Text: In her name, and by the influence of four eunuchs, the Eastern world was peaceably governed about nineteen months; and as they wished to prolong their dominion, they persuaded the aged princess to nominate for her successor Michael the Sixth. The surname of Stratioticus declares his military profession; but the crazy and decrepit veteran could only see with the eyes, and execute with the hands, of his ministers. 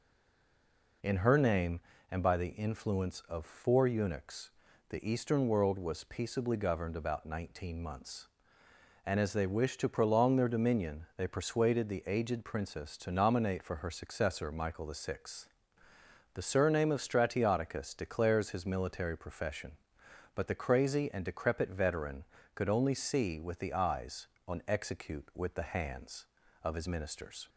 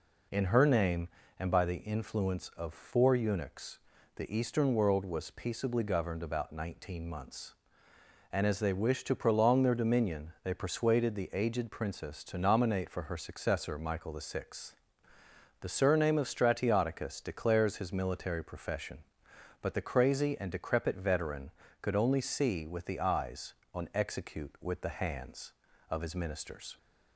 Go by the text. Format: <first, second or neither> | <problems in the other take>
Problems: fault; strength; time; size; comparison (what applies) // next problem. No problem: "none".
second | stays silent before the first word; until 1.0 s; 1.0 s long